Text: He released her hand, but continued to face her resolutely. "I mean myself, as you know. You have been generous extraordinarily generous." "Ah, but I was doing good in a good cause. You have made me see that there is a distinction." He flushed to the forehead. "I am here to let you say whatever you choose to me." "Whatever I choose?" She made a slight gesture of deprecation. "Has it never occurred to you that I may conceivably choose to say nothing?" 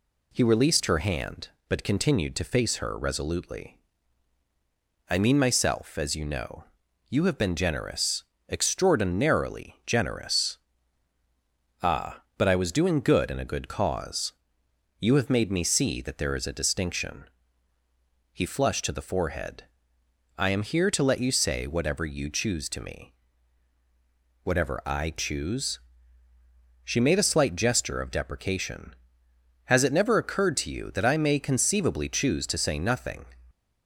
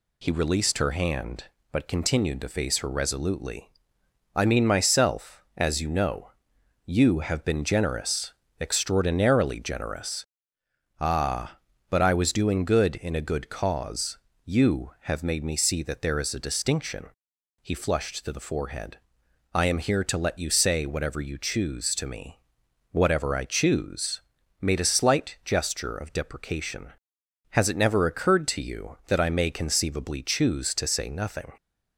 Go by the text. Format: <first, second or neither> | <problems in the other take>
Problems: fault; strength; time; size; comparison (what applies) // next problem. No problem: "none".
first | pauses between "generous" and "extraordinarily"; slight; at 8.3 s; 0.28 s long; slight in the first // skips "She"; at 24.4 s